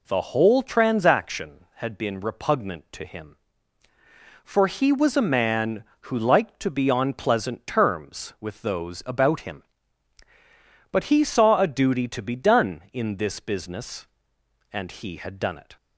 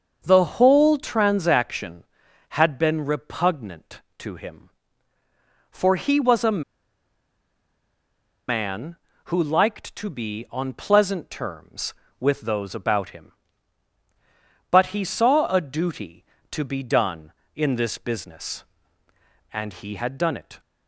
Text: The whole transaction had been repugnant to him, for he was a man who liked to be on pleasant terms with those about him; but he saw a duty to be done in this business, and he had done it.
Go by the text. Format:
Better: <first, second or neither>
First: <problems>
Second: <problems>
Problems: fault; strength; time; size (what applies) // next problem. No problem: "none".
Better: first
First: none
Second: starts louder than the rest; until 1.2 s; 6.5 dB // pauses between "a" and "man"; strong; at 6.6 s; 1.8 s long